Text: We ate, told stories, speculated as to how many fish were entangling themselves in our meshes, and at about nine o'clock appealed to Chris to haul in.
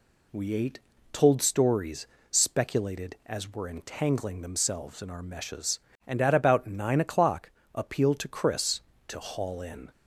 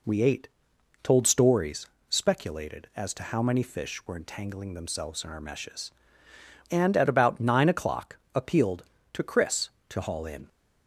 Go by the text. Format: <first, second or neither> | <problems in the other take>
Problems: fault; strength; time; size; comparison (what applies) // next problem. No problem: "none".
second | skips "to how many fish"; at 3.5 s // pauses between "o'clock" and "appealed"; slight; at 7.4 s; 0.24 s long; slight in the second